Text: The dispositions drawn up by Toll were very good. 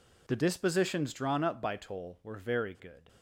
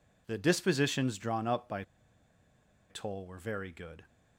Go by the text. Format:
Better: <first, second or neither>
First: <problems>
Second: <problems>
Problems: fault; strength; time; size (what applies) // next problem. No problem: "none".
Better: first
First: none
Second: pauses between "by" and "Toll"; at 1.8 s; 1.0 s long